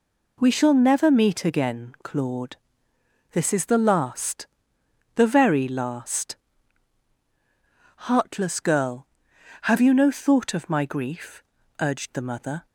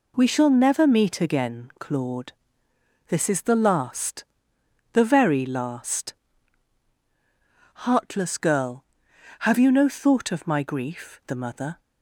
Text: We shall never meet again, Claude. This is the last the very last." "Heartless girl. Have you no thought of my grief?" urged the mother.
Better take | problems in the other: first | pauses between "last" and "the"; noticeable; at 4.2 s; 0.70 s long; noticeable in the first // skips "urged"; at 11.2 s

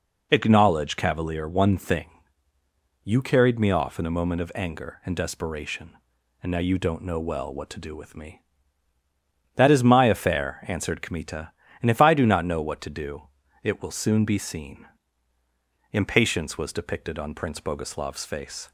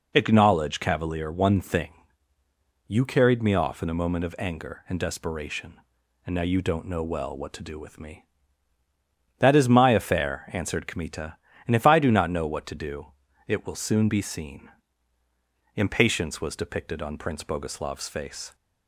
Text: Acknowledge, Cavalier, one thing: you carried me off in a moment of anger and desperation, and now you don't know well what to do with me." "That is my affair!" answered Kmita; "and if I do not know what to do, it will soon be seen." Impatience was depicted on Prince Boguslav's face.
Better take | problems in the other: neither | none

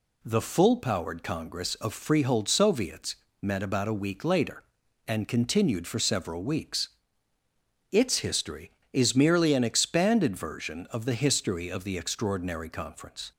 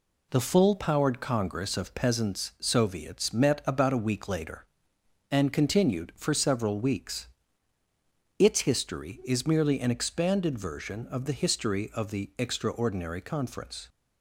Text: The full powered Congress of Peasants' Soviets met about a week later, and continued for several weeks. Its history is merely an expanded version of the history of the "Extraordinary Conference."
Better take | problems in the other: second | says "Freehold" for "Peasants"; at 1.9 s // pauses between "Soviets" and "met"; slight; at 3.1 s; 0.26 s long

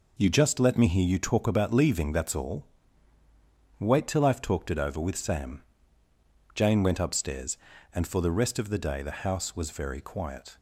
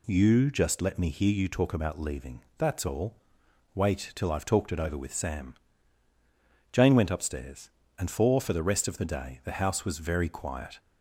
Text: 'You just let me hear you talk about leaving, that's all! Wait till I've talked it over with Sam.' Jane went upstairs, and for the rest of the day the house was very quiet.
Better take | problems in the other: first | says "for" twice; at 8.3 s

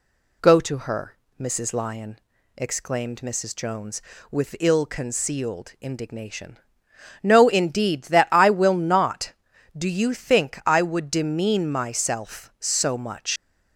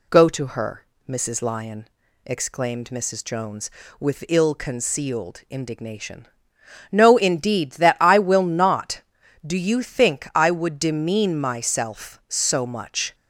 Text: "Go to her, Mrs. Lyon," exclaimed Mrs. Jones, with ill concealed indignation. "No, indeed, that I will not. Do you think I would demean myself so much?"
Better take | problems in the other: second | leaves "much" unfinished; at 13.3 s; 100 ms

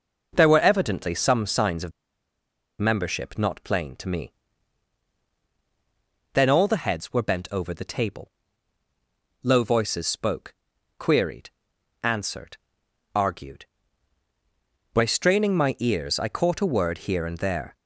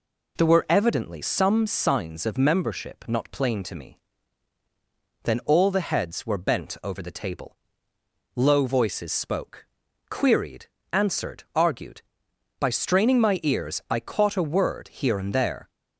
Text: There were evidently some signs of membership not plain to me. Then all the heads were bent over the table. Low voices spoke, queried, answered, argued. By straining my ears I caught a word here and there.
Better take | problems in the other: second | pauses between "of" and "membership"; noticeable; at 1.9 s; 0.88 s long

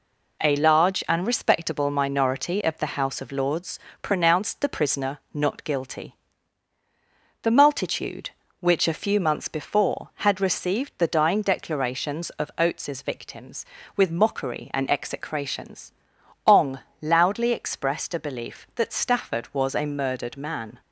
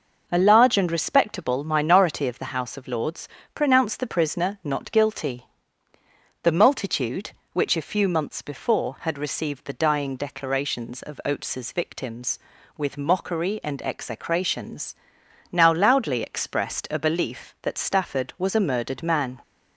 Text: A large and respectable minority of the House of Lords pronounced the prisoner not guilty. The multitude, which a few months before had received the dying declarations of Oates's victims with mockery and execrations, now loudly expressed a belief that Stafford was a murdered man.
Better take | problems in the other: second | pauses between "Lords" and "pronounced"; slight; at 3.7 s; 0.24 s long; slight in the second // says "ong" for "now"; at 16.4 s

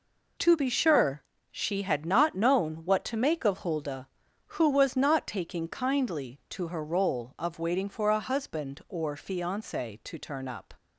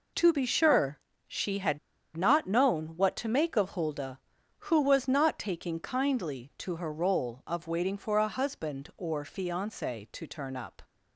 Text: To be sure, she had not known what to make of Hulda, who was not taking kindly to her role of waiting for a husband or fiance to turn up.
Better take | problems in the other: first | pauses between "had" and "not"; at 1.7 s; 0.38 s long

